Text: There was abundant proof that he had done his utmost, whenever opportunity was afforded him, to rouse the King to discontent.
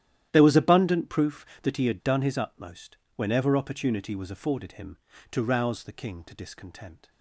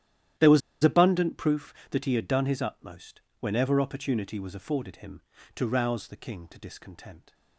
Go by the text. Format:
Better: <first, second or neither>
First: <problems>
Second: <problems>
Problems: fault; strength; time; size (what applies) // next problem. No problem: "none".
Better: first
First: starts louder than the rest; strong; until 1.3 s; 11.5 dB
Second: starts louder than the rest; strong; until 1.6 s; 11.5 dB // pauses between "was" and "abundant"; slight; at 0.6 s; 0.23 s long